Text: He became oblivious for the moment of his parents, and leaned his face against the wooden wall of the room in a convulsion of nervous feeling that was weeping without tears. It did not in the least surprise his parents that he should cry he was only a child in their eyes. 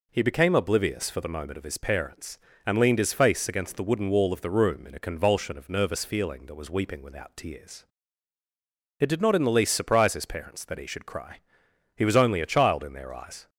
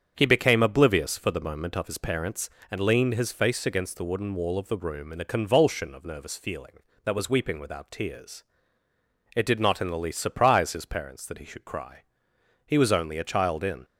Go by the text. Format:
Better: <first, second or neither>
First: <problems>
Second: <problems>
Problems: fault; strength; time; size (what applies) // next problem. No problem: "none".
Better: first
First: pauses between "cry" and "he"; noticeable; at 11.3 s; 0.58 s long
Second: starts louder than the rest; strong; until 1.1 s; 7.5 dB // pauses between "cry" and "he"; noticeable; at 12.0 s; 0.66 s long // stops before "their eyes"; at 13.8 s